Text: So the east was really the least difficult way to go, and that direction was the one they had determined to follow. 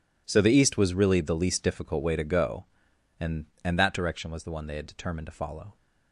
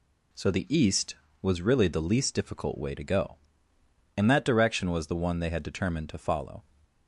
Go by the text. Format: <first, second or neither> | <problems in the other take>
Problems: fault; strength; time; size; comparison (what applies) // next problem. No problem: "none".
second | says "and" twice; at 3.6 s